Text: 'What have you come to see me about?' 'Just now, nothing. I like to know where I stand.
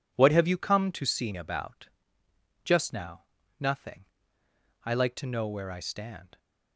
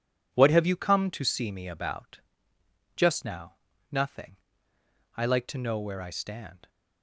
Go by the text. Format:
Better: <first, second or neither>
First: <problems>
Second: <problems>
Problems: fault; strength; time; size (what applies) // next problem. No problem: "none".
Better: second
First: skips "me"; at 1.3 s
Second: none